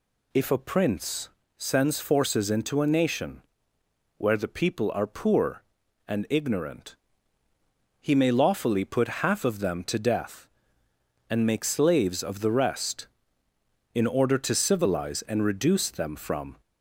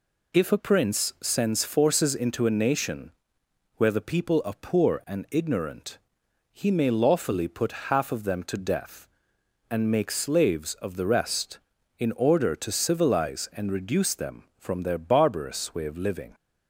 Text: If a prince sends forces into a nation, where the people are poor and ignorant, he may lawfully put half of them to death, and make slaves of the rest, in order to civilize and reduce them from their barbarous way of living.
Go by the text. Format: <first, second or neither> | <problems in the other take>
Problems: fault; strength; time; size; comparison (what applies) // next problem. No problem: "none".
second | pauses between "prince" and "sends"; slight; at 1.2 s; 0.28 s long // stops before "their barbarous way of living"; at 16.6 s